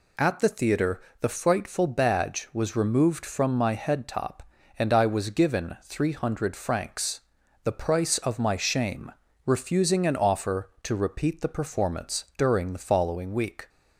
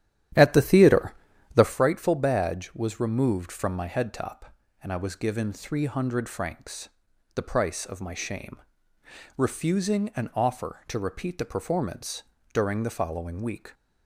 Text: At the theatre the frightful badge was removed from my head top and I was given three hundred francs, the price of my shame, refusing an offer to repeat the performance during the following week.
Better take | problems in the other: first | starts louder than the rest; strong; until 1.8 s; 11 dB // pauses between "theatre" and "the"; at 1.1 s; 0.42 s long; slight in the first // pauses between "performance" and "during"; slight; at 12.2 s; 0.28 s long

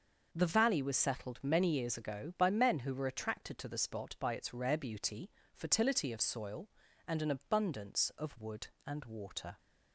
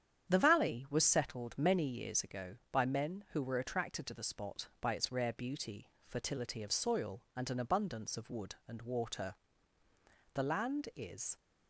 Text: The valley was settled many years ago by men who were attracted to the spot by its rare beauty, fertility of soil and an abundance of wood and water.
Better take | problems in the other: first | starts louder than the rest; strong; until 1.3 s; 9 dB // goes on to say "The land is"; noticeable; from 10.3 s on; 1.0 s long

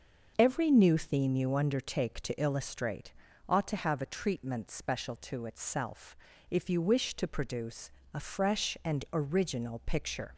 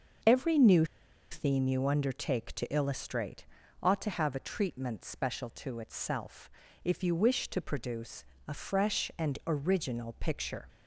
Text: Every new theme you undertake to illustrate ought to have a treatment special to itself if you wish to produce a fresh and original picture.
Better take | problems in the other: first | starts louder than the rest; noticeable; until 1.7 s; 6 dB // pauses between "new" and "theme"; at 0.8 s; 0.45 s long // pauses between "illustrate" and "ought"; at 3.4 s; 0.38 s long; also in the first // pauses between "itself" and "if"; slight; at 6.4 s; 0.34 s long; slight in the first // pauses between "produce" and "a"; slight; at 8.2 s; 0.24 s long; slight in the first

